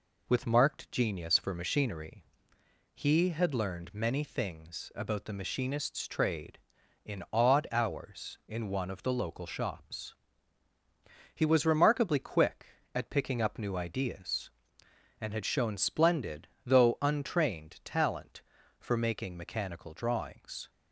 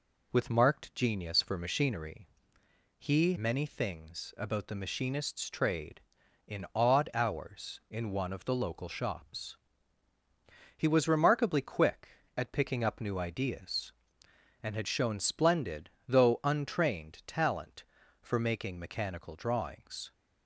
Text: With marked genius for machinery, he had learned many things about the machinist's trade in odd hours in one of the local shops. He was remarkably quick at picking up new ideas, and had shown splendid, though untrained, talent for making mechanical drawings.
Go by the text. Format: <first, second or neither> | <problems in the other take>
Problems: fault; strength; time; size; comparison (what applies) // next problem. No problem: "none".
first | skips "had learned"; at 3.3 s